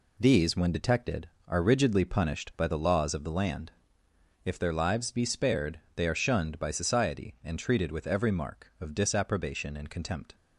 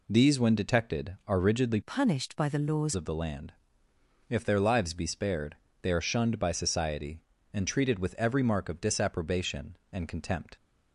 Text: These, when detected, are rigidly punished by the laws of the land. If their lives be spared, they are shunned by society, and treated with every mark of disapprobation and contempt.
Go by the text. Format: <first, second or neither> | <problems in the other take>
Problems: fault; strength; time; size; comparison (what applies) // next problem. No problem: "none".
first | changes voice from "punished" to "laws"; from 1.8 to 2.9 s; 1.1 s long